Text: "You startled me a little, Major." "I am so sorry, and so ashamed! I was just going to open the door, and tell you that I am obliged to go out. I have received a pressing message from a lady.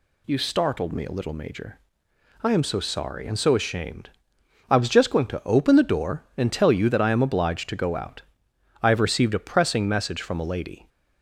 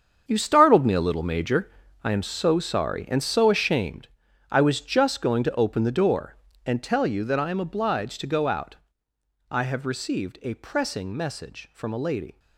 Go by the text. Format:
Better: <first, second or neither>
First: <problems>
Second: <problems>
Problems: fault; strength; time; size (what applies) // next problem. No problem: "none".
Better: first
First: none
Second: gets quieter; strong; throughout; 12.5 dB